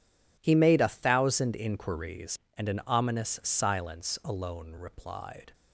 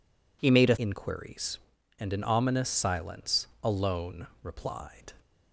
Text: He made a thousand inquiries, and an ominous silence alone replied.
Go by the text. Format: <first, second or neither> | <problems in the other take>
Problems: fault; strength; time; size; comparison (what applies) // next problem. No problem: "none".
first | skips "thousand"; at 0.7 s // pauses between "silence" and "alone"; slight; at 3.4 s; 0.16 s long // pauses between "alone" and "replied"; slight; at 4.2 s; 0.16 s long